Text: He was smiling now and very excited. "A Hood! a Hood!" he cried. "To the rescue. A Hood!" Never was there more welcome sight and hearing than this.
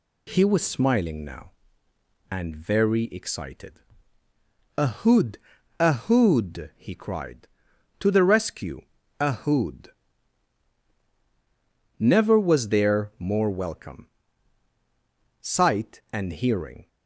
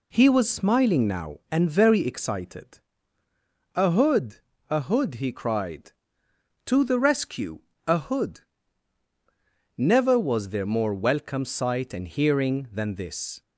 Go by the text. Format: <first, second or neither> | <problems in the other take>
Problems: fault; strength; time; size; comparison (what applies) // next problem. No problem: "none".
second | pauses between "welcome" and "sight"; strong; at 14.0 s; 1.3 s long // stops before "than this"; at 16.8 s